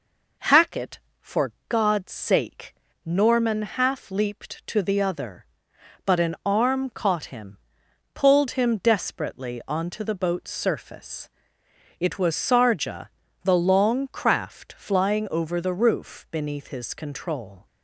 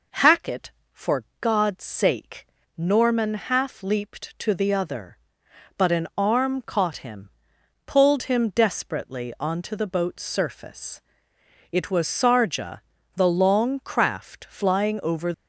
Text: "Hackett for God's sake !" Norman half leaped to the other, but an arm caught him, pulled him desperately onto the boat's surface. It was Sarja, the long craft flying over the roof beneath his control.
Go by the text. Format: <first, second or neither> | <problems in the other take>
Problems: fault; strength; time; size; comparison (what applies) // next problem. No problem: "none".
first | pauses between "for" and "God's"; slight; at 1.2 s; 0.16 s long; slight in the first // stops before "the roof beneath his control"; at 15.3 s